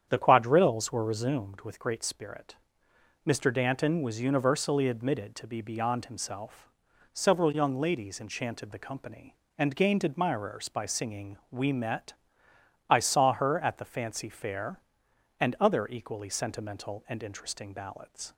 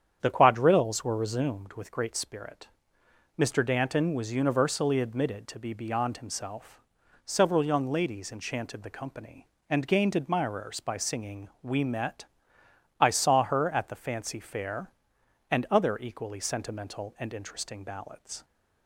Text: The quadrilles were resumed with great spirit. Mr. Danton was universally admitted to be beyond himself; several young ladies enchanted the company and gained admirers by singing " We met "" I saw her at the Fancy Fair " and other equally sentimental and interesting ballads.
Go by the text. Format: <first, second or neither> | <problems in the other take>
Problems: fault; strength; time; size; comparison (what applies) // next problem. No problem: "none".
neither | starts louder than the rest; strong; the same in both